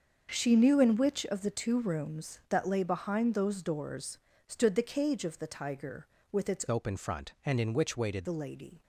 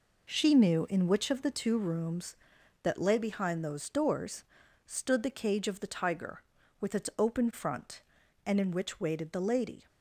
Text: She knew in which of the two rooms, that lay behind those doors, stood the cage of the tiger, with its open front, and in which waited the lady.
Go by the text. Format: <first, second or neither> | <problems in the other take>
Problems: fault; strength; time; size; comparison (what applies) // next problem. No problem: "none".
second | starts louder than the rest; until 1.3 s; 6.5 dB // changes voice from "open" to "waited"; from 6.6 to 8.2 s; 1.6 s long